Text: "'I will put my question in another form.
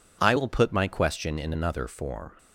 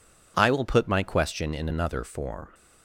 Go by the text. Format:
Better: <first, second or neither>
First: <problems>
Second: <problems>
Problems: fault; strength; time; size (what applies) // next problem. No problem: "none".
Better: neither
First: none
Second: none